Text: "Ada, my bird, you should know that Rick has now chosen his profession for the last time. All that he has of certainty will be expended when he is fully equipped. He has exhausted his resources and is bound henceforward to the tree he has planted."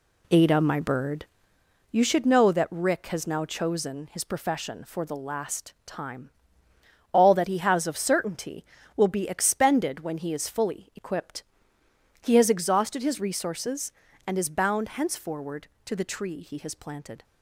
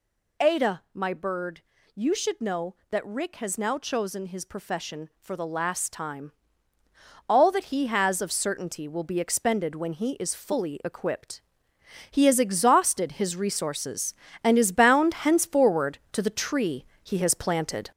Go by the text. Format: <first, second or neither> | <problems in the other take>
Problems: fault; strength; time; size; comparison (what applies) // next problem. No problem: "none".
first | gets louder; noticeable; throughout; 5 dB // pauses between "tree" and "he"; slight; at 16.8 s; 0.18 s long